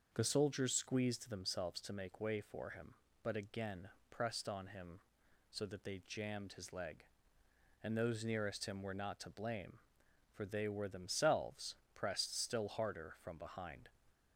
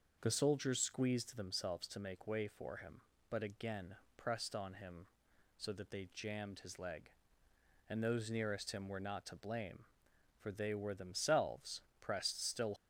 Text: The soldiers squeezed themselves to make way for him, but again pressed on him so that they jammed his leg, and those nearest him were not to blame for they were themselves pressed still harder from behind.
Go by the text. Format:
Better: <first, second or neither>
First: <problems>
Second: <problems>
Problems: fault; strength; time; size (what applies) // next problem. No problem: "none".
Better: first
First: starts louder than the rest; until 1.1 s; 6.5 dB // pauses between "again" and "pressed"; slight; at 3.8 s; 0.22 s long // pauses between "themselves" and "pressed"; slight; at 11.7 s; 0.18 s long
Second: starts louder than the rest; until 1.2 s; 6.5 dB // pauses between "again" and "pressed"; slight; at 3.9 s; 0.22 s long // pauses between "themselves" and "pressed"; slight; at 11.8 s; 0.18 s long // stops before "harder from behind"; at 12.7 s